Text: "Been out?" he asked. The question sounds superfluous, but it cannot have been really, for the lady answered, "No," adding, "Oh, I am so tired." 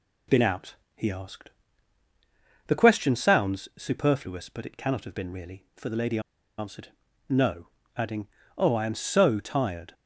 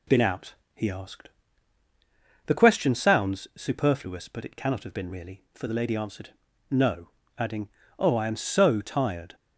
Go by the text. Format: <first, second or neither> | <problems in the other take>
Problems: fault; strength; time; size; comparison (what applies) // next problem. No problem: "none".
second | pauses between "lady" and "answered"; at 6.1 s; 0.39 s long